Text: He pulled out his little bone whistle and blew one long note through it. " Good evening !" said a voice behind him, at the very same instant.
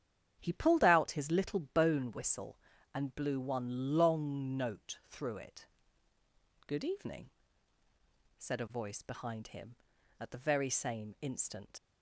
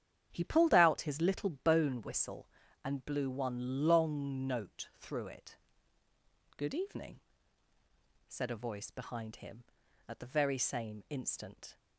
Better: second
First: starts louder than the rest; strong; until 1.3 s; 10.5 dB // leaves "instant" unfinished; at 11.7 s; 105 ms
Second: starts louder than the rest; strong; until 1.3 s; 10.5 dB

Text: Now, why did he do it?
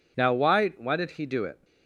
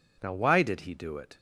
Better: second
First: says "why" twice; at 0.7 s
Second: none

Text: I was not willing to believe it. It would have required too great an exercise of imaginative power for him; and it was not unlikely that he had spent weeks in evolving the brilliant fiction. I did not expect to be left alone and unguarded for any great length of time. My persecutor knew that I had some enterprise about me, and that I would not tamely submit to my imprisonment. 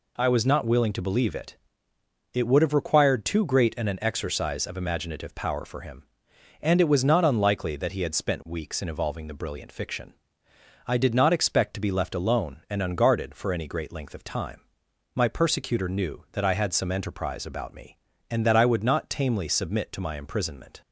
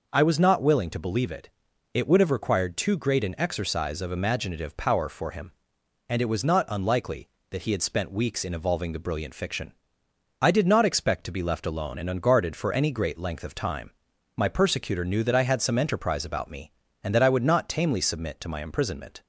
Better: second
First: says "an" twice; at 3.8 s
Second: none

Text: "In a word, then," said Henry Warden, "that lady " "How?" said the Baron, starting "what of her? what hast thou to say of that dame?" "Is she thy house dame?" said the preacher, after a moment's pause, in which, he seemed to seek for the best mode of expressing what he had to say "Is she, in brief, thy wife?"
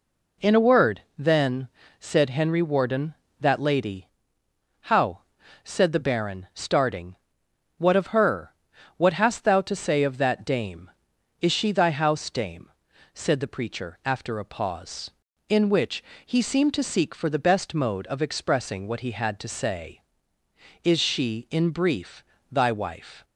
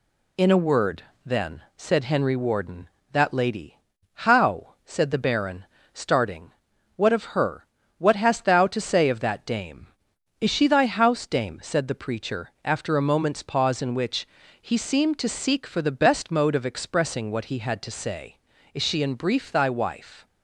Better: second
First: pauses between "starting" and "what"; noticeable; at 7.1 s; 0.62 s long // skips "moment's"; at 14.4 s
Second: pauses between "starting" and "what"; at 6.5 s; 0.44 s long

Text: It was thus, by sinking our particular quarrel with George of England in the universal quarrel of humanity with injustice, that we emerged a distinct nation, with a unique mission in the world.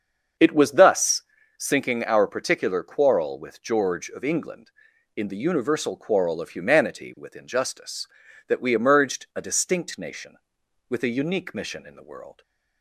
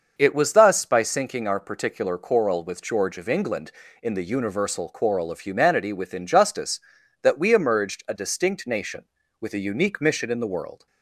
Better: second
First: starts louder than the rest; until 1.7 s; 6.5 dB // skips "by"; at 1.4 s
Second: starts louder than the rest; until 1.1 s; 6 dB

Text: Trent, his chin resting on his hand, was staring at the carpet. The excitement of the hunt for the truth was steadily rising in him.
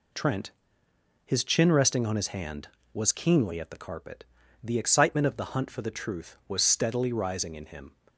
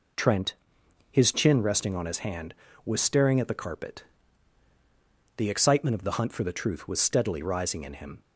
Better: second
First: says "keenly" for "staring"; at 3.1 s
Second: none

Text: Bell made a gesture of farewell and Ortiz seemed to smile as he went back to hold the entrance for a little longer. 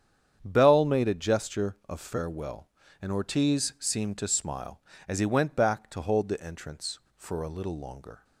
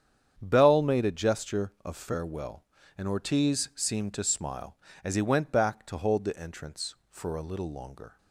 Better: neither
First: starts louder than the rest; strong; until 1.4 s; 8.5 dB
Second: starts louder than the rest; strong; until 1.4 s; 8.5 dB

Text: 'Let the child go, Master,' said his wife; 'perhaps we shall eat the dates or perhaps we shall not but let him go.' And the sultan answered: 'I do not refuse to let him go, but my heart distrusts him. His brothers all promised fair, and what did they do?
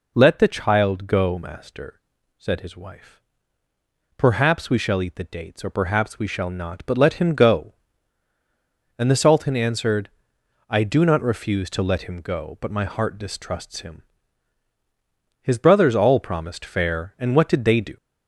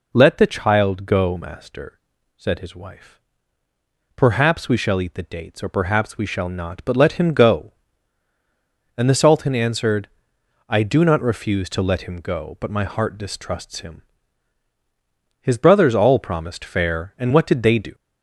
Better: neither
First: none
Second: none

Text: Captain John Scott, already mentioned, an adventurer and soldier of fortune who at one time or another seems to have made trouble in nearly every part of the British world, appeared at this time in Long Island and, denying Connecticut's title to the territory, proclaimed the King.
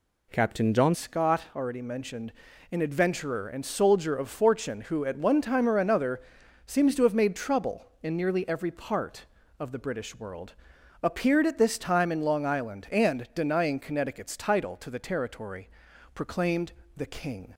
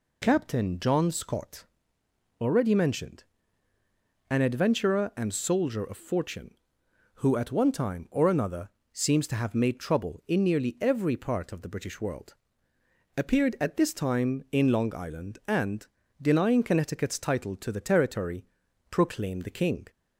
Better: second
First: changes voice at "Scott"; from 0.9 s on; 16.6 s long // pauses between "another" and "seems"; noticeable; at 6.1 s; 0.46 s long // pauses between "proclaimed" and "the"; slight; at 16.7 s; 0.24 s long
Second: pauses between "another" and "seems"; slight; at 8.6 s; 0.24 s long

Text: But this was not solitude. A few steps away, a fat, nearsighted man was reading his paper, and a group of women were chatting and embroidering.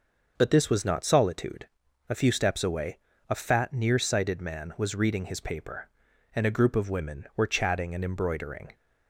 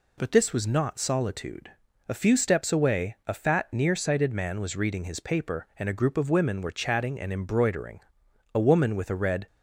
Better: first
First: none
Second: goes on to say "A woman with a red"; noticeable; from 8.5 s on; 0.94 s long

